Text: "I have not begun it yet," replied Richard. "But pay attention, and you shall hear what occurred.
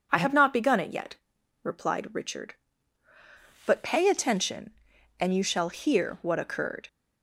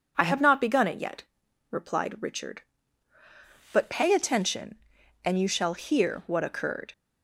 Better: neither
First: none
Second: none

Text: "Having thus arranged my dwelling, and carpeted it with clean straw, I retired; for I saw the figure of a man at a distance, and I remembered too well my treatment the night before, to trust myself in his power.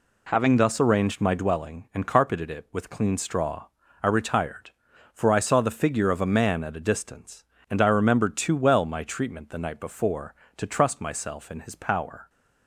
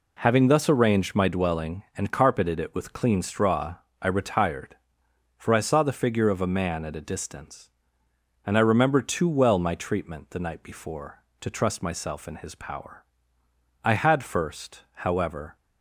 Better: first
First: none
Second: goes on to say "I had first however"; strong; from 13.8 s on; 1.7 s long

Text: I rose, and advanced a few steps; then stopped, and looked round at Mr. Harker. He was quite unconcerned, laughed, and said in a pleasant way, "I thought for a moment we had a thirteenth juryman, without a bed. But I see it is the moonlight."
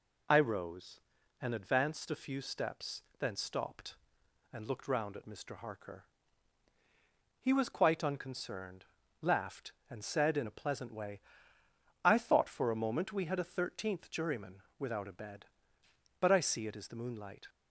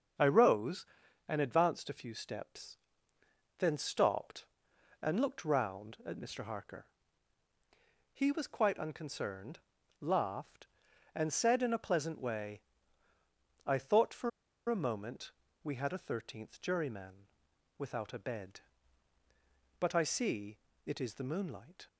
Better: first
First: none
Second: starts louder than the rest; until 1.6 s; 7 dB // pauses between "for" and "a"; at 14.2 s; 0.39 s long // pauses between "moment" and "we"; slight; at 15.3 s; 0.32 s long // pauses between "see" and "it"; slight; at 20.5 s; 0.28 s long

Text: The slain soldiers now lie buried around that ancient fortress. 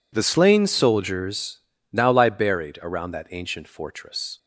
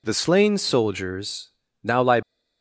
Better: first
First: pauses between "soldiers" and "now"; slight; at 1.5 s; 0.34 s long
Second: pauses between "soldiers" and "now"; slight; at 1.4 s; 0.34 s long // stops before "buried around that ancient fortress"; at 2.2 s

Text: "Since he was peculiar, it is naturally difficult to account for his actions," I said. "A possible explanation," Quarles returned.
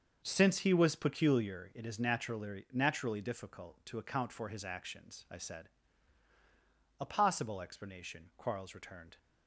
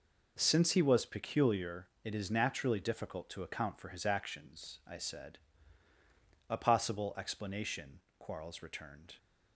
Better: second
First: starts louder than the rest; until 1.2 s; 6.5 dB // says "naturally" twice; at 2.7 s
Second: none

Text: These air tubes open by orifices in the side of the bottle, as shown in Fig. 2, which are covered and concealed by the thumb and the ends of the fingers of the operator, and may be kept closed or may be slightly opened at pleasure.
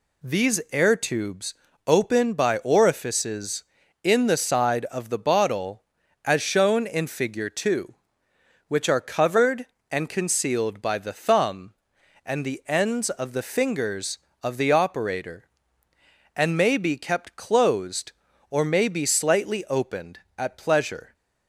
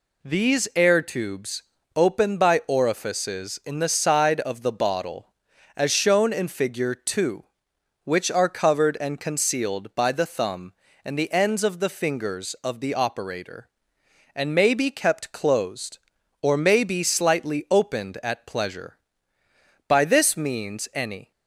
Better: first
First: pauses between "tubes" and "open"; slight; at 1.5 s; 0.32 s long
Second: pauses between "tubes" and "open"; slight; at 1.6 s; 0.34 s long // goes on to say "By this means any"; from 19.8 s on; 1.4 s long

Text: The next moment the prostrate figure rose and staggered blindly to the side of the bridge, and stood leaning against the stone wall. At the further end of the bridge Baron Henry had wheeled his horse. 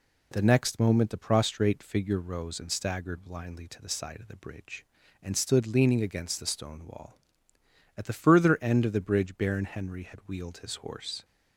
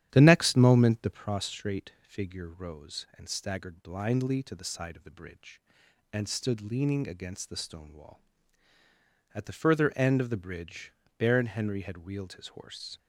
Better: first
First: none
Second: starts louder than the rest; strong; until 1.3 s; 11 dB // pauses between "bridge" and "Baron"; slight; at 10.9 s; 0.26 s long

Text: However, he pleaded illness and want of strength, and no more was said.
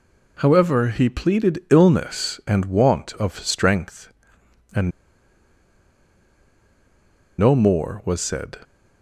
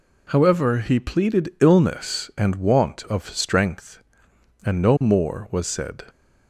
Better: second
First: pauses between "and" and "no"; strong; at 4.9 s; 2.4 s long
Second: none

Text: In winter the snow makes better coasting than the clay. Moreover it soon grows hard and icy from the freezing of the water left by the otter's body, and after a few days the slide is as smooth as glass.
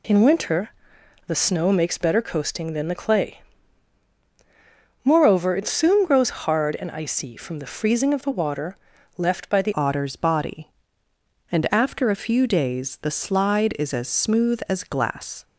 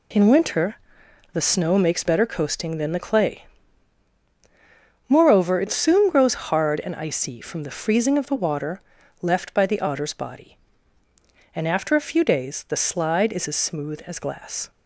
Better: second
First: pauses between "winter" and "the"; noticeable; at 0.6 s; 0.56 s long // pauses between "water" and "left"; at 8.7 s; 0.40 s long // changes voice at "otter's"; from 9.7 s on; 5.7 s long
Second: pauses between "winter" and "the"; noticeable; at 0.7 s; 0.56 s long // pauses between "water" and "left"; at 8.8 s; 0.40 s long

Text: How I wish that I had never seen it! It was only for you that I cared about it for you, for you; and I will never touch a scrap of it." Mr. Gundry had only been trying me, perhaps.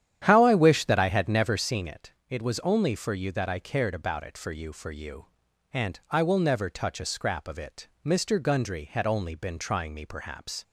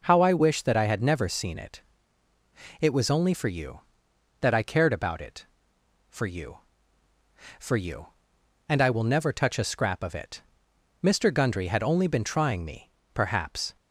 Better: second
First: starts louder than the rest; strong; until 1.8 s; 10 dB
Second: none

